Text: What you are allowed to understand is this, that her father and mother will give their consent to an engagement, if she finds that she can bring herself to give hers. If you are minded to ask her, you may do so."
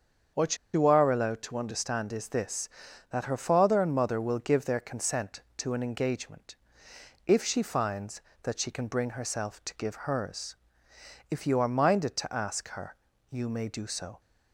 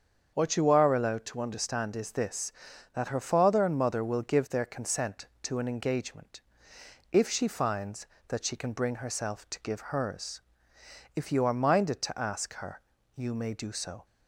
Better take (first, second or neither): second